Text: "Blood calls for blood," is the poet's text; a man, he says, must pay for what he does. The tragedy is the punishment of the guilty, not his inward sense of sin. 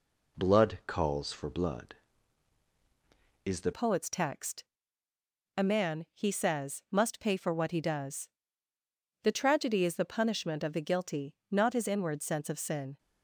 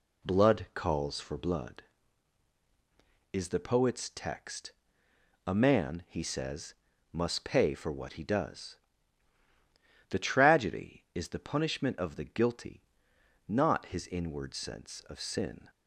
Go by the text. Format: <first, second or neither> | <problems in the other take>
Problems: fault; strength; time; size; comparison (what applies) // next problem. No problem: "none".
second | changes voice at "poet's"; from 3.7 s on; 9.2 s long